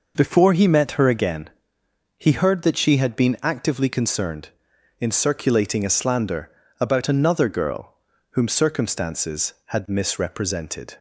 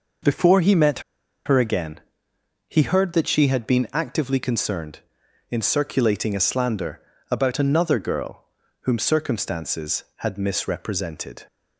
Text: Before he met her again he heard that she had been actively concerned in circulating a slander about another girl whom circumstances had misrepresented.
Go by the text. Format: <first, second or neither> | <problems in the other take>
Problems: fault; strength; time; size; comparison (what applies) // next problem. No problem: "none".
first | pauses between "met" and "her"; noticeable; at 0.9 s; 0.46 s long // pauses between "again" and "he"; noticeable; at 2.0 s; 0.68 s long; noticeable in the first // pauses between "slander" and "about"; slight; at 6.9 s; 0.32 s long; slight in the first // pauses between "girl" and "whom"; at 8.4 s; 0.38 s long; also in the first